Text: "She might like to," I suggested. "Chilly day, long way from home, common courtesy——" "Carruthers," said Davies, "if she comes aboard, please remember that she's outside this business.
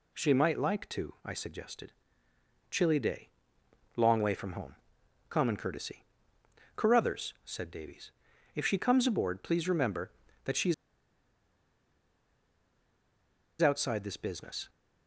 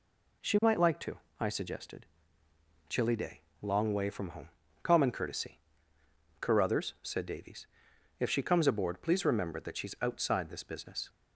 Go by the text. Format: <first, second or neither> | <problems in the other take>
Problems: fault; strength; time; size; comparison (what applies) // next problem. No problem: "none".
second | pauses between "she's" and "outside"; strong; at 10.7 s; 2.8 s long